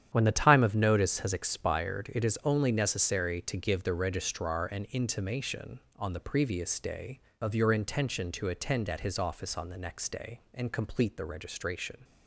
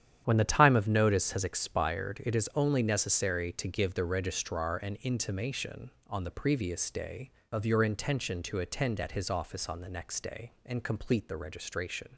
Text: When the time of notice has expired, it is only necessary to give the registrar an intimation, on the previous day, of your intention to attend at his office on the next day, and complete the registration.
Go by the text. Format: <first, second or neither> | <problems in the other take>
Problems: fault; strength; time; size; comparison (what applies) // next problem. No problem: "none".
neither | starts louder than the rest; strong; the same in both